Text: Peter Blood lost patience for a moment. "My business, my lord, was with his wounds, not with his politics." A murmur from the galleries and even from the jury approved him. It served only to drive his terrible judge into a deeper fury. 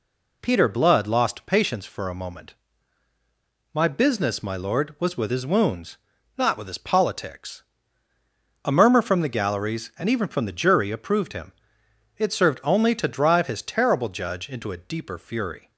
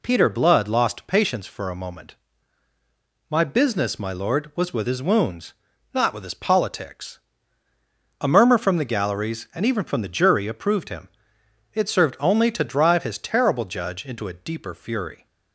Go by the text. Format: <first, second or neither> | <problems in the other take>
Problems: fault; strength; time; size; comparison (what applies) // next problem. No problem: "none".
neither | none